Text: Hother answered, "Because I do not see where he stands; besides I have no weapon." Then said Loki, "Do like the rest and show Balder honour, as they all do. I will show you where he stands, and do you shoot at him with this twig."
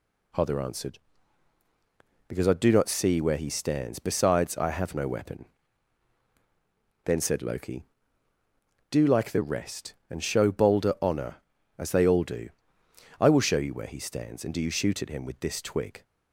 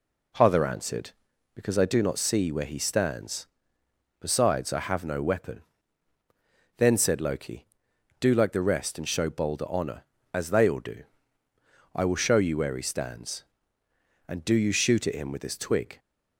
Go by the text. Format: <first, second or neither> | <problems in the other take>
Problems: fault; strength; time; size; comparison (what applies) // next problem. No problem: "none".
neither | none